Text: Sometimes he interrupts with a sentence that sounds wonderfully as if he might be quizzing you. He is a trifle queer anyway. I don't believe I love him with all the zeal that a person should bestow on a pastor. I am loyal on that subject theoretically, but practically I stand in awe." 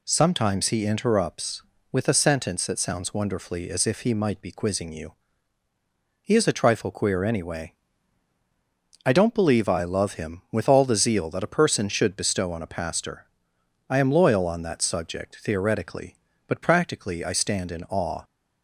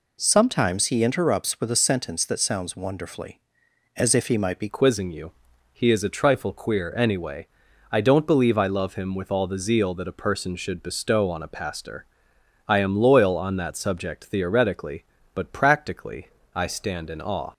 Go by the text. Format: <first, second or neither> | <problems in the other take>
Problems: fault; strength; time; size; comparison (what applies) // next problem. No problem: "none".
first | changes voice at "quizzing"; from 4.6 s on; 12.9 s long // pauses between "practically" and "I"; slight; at 16.2 s; 0.30 s long